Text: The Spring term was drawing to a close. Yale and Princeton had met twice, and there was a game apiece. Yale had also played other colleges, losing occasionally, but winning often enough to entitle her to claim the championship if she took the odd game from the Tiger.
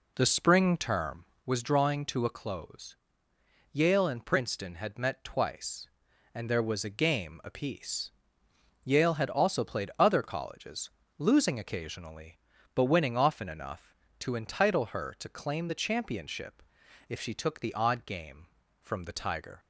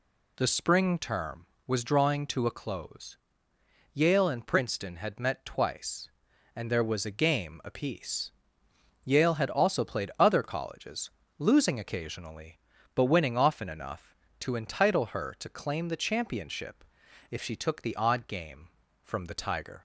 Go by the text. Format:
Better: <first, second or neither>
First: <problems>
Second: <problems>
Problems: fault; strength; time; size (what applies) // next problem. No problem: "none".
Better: second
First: starts louder than the rest; slight; until 1.4 s; 3 dB // pauses between "championship" and "if"; noticeable; at 16.6 s; 0.48 s long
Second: pauses between "championship" and "if"; noticeable; at 16.8 s; 0.48 s long